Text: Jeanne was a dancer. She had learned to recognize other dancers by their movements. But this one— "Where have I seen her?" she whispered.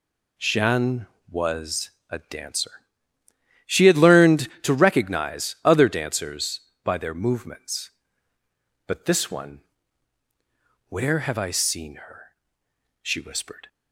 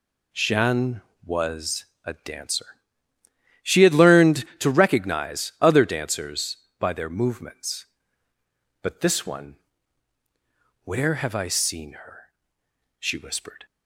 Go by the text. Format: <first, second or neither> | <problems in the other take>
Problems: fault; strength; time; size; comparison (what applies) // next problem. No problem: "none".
neither | pauses between "was" and "a"; slight; the same in both